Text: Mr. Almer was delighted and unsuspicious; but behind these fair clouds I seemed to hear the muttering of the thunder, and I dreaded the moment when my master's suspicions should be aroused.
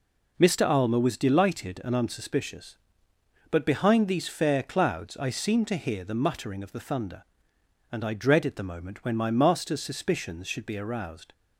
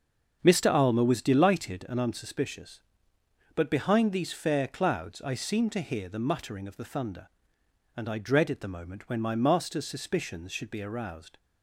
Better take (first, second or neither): first